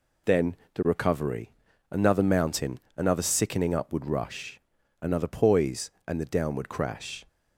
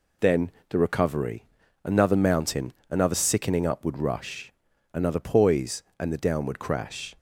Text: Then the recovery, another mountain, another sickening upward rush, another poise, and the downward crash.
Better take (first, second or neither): neither